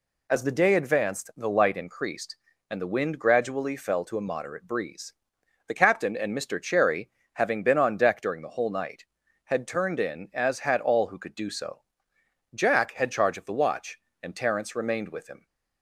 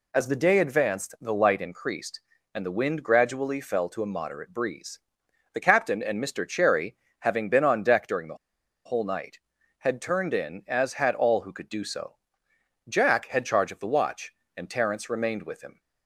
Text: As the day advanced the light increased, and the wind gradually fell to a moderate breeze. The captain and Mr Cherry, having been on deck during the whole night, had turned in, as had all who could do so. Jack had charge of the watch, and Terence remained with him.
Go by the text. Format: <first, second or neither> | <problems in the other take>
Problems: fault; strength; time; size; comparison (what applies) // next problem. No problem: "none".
first | pauses between "the" and "whole"; noticeable; at 8.3 s; 0.49 s long